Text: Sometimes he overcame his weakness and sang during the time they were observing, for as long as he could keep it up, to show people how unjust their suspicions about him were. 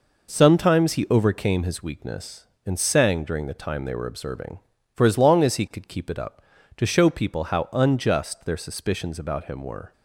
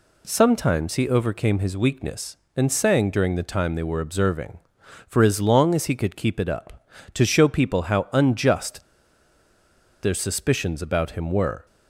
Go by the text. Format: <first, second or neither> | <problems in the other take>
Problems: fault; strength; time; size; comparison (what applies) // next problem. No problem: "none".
first | pauses between "unjust" and "their"; at 8.8 s; 1.2 s long